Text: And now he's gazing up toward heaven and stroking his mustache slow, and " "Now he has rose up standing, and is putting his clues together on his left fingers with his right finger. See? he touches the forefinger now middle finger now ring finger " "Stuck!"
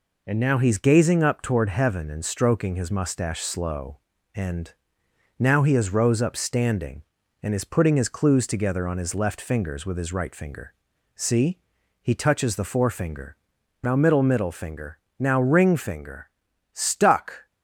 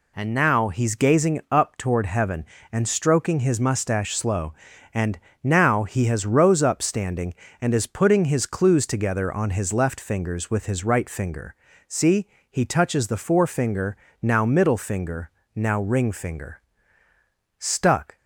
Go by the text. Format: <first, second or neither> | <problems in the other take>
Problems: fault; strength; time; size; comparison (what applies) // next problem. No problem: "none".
second | pauses between "forefinger" and "now"; noticeable; at 13.3 s; 0.48 s long; slight in the second // says "middle" twice; at 14.2 s // pauses between "finger" and "now"; slight; at 14.9 s; 0.20 s long; slight in the second